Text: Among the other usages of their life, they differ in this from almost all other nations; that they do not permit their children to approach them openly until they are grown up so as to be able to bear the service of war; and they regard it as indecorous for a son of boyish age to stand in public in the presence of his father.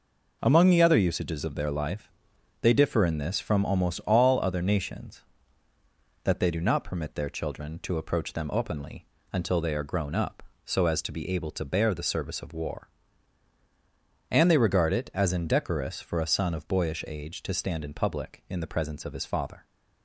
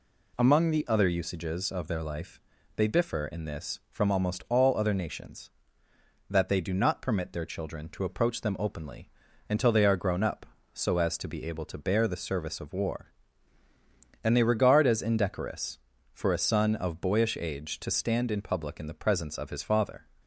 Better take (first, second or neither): first